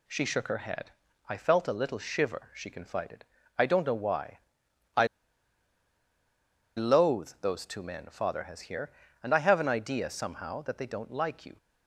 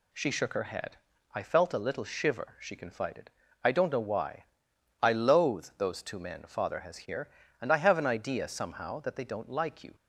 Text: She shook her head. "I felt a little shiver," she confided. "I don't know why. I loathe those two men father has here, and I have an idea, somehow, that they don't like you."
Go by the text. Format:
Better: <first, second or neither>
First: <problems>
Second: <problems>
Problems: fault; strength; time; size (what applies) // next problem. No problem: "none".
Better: second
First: pauses between "I" and "loathe"; strong; at 5.0 s; 1.6 s long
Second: none